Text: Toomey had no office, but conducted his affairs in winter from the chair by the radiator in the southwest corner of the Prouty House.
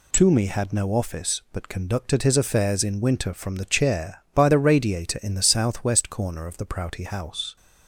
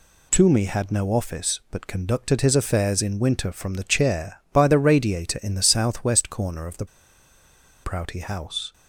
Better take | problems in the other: first | pauses between "the" and "Prouty"; at 6.8 s; 0.98 s long

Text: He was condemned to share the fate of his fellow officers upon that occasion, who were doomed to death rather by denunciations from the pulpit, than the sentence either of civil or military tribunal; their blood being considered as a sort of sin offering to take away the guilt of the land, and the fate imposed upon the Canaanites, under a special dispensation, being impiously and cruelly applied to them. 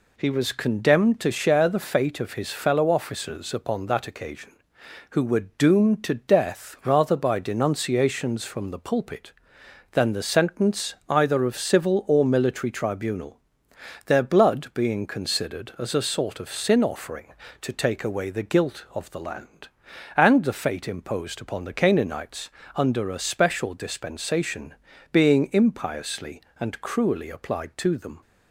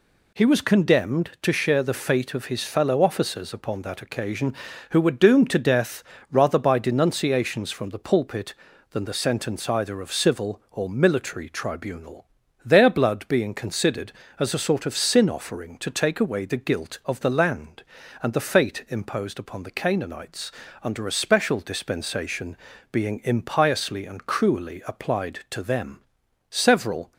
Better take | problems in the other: first | pauses between "death" and "rather"; slight; at 6.0 s; 0.28 s long // goes on to say "Several"; noticeable; from 26.4 s on; 0.64 s long

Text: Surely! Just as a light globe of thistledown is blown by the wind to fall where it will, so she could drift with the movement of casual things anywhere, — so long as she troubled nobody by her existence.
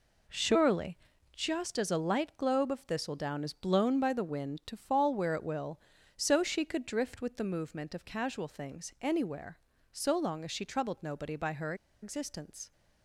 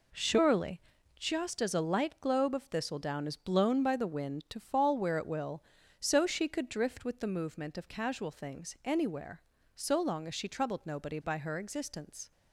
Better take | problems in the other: second | pauses between "her" and "existence"; slight; at 11.7 s; 0.28 s long

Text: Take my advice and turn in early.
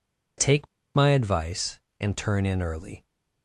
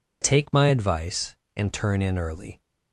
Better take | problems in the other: second | pauses between "Take" and "my"; slight; at 0.6 s; 0.27 s long

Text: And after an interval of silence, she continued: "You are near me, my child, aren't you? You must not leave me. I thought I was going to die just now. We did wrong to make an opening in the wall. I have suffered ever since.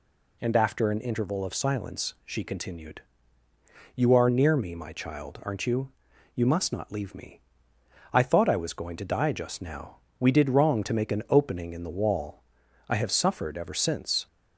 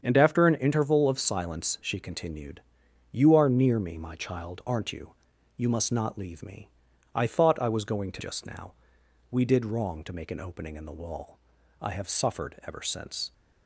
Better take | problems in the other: first | starts louder than the rest; strong; until 1.0 s; 7.5 dB // skips "die"; at 8.2 s

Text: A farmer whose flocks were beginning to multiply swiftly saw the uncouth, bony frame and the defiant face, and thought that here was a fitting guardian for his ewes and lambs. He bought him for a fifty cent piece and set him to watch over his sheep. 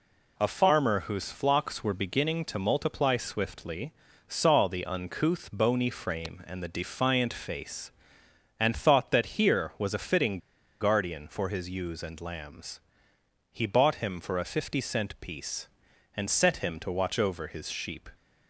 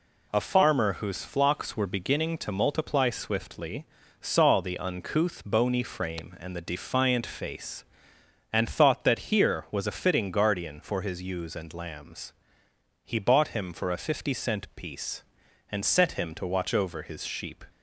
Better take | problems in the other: second | pauses between "swiftly" and "saw"; slight; at 3.9 s; 0.34 s long; slight in the second // pauses between "fitting" and "guardian"; at 10.3 s; 0.43 s long

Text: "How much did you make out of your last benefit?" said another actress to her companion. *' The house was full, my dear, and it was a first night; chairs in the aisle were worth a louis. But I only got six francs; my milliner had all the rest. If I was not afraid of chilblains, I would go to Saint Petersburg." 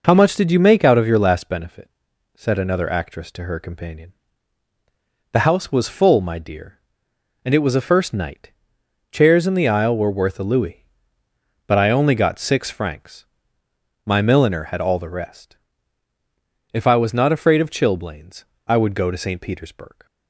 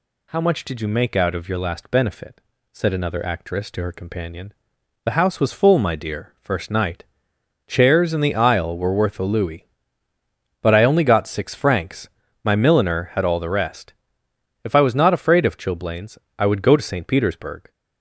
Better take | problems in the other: first | skips "and it was a"; at 6.3 s

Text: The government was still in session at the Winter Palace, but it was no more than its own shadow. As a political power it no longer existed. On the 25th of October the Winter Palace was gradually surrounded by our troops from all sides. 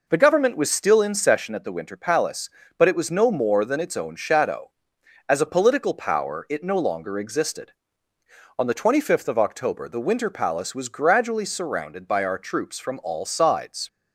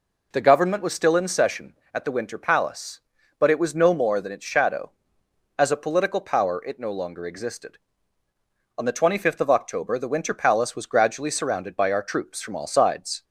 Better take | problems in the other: first | skips "own"; at 4.4 s

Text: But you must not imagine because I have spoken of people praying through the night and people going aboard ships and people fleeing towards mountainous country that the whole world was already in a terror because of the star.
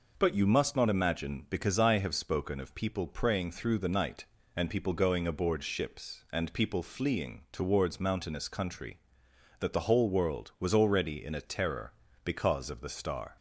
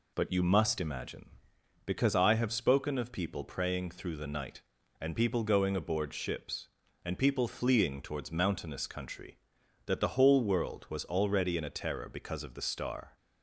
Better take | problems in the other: first | skips "not"; at 0.8 s

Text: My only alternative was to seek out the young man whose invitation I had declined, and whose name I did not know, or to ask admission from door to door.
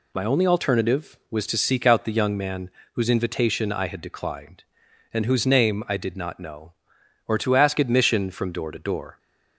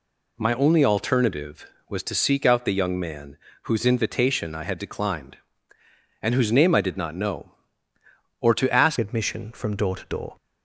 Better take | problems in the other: first | pauses between "man" and "whose"; slight; at 3.3 s; 0.26 s long; slight in the first // changes voice at "admission"; from 8.9 s on; 1.4 s long

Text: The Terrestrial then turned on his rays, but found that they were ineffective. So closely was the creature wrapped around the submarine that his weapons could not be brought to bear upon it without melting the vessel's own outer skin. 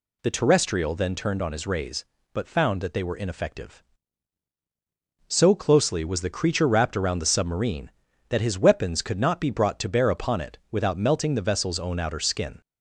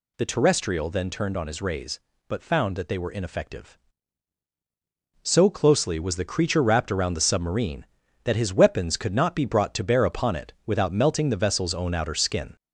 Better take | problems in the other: first | gets louder; slight; throughout; 3.5 dB

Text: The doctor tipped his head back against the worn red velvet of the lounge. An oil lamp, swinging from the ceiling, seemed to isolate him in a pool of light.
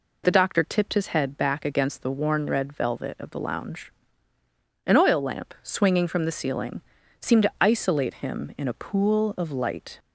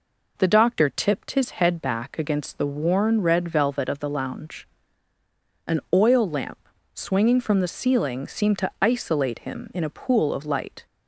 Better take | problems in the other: neither | none

